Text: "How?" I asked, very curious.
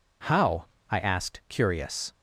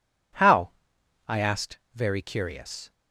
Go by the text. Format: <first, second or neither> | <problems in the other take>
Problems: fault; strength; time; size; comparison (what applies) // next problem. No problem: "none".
second | skips "very"; at 1.4 s